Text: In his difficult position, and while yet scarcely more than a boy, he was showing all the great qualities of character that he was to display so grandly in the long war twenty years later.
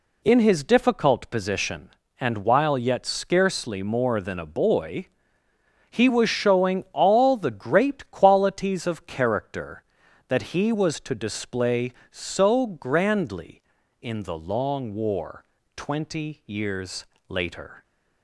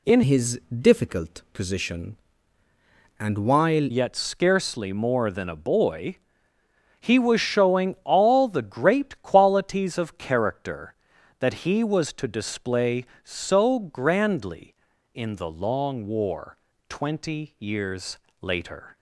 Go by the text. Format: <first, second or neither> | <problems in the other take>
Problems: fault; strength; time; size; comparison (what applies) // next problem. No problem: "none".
first | changes voice from "his" to "while"; from 0.2 to 3.8 s; 3.6 s long // pauses between "war" and "twenty"; slight; at 16.5 s; 0.32 s long; slight in the first // pauses between "years" and "later"; slight; at 18.1 s; 0.20 s long; slight in the first